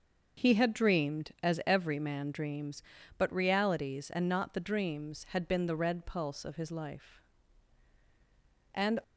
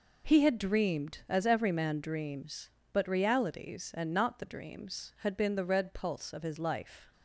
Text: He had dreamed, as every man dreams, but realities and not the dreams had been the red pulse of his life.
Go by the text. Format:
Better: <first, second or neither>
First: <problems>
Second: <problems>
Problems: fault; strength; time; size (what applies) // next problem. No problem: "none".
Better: second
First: starts louder than the rest; until 1.4 s; 6 dB // goes on to say "And"; slight; from 8.7 s on; 0.28 s long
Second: none